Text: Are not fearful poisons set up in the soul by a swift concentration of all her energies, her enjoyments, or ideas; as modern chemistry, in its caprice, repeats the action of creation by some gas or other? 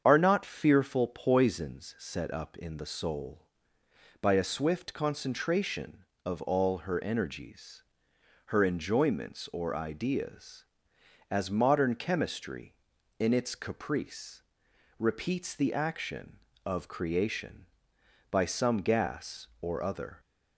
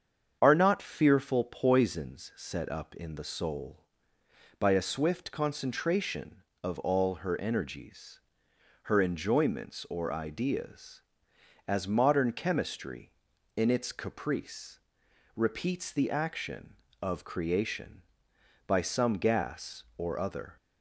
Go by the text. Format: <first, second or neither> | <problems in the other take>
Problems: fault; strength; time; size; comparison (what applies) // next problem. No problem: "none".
neither | starts louder than the rest; strong; the same in both